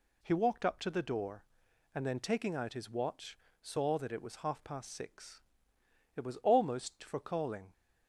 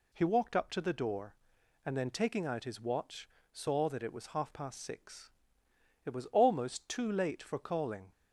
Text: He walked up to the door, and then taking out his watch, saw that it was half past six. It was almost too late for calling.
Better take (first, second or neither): second